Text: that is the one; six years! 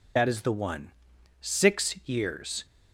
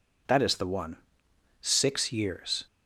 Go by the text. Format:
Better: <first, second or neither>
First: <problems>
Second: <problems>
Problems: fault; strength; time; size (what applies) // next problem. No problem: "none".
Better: second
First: loses the start of "that"; at 0.1 s; 45 ms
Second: none